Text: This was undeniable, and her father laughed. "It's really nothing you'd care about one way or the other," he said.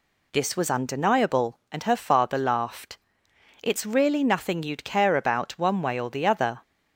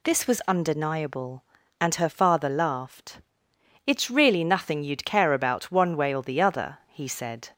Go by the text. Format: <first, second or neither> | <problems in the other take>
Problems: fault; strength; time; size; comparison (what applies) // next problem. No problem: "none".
second | stops before "he said"; at 6.6 s